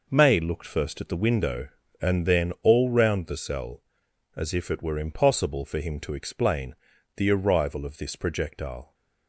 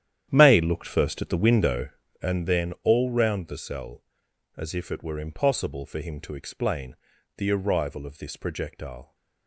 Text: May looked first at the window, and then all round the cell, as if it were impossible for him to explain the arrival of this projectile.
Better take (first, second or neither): first